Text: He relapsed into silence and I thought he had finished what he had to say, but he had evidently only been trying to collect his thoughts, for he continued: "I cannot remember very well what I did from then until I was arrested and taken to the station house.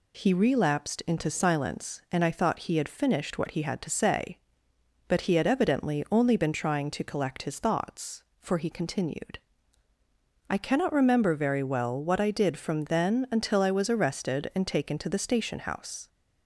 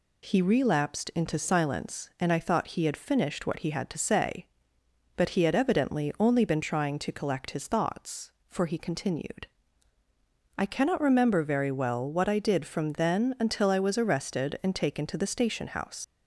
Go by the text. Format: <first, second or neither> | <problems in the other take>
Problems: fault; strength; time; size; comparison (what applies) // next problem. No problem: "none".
first | leaves "house" unfinished; at 16.0 s; 115 ms